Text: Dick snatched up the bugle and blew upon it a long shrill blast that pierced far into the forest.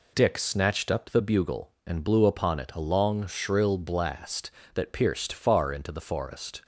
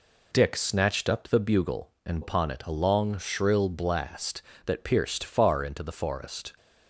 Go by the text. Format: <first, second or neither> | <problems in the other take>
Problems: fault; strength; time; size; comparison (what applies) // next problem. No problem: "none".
first | skips "blew"; at 2.2 s